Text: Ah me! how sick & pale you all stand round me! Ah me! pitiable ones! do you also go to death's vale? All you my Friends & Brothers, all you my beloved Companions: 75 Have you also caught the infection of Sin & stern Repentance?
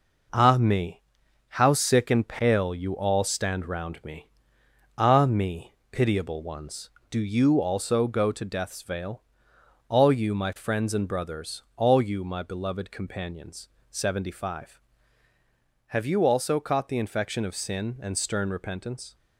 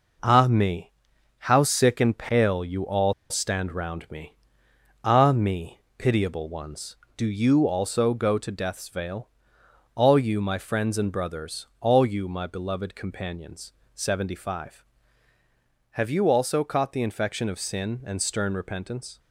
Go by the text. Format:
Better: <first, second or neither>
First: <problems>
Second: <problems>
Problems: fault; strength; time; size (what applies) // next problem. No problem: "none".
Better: first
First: none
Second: pauses between "all" and "stand"; slight; at 3.1 s; 0.17 s long